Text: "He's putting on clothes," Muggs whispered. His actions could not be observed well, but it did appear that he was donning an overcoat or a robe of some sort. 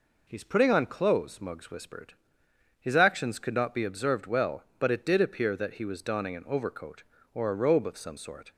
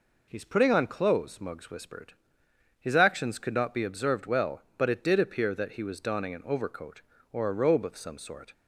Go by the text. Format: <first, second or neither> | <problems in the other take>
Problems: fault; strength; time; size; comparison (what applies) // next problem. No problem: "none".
neither | none